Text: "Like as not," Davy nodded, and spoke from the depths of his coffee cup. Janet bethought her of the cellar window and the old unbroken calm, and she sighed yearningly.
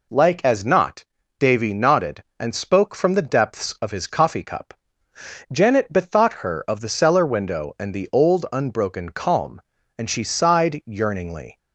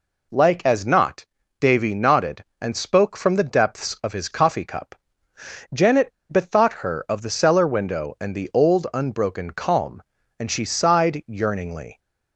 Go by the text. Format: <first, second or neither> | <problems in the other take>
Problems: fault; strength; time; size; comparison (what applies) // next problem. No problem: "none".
first | pauses between "Janet" and "bethought"; slight; at 6.1 s; 0.20 s long